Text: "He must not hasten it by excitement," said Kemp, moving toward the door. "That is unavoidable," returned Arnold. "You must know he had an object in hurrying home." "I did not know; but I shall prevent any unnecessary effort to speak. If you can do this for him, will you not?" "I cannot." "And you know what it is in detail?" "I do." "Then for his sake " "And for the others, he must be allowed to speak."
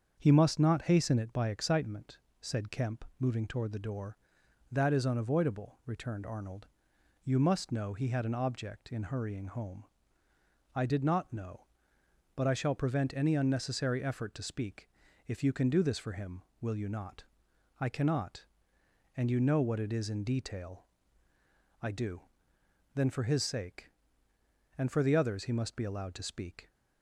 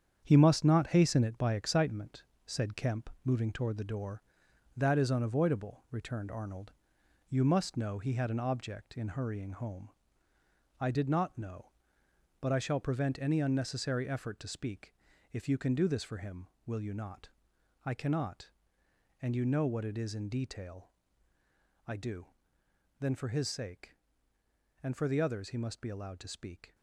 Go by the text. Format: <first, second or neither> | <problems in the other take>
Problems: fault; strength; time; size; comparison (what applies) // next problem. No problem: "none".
first | gets quieter; strong; throughout; 11 dB // starts louder than the rest; strong; until 1.2 s; 8 dB; also in the first